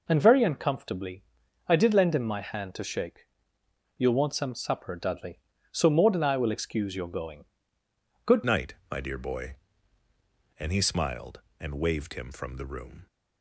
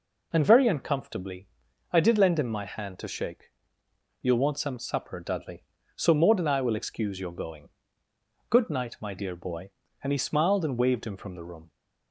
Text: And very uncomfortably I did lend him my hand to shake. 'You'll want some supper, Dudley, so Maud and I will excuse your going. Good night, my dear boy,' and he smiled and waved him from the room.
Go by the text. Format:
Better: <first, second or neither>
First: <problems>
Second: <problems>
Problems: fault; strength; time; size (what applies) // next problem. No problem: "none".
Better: second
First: pauses between "uncomfortably" and "I"; at 1.2 s; 0.44 s long // changes voice at "night"; from 8.4 s on; 4.6 s long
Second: pauses between "uncomfortably" and "I"; at 1.4 s; 0.44 s long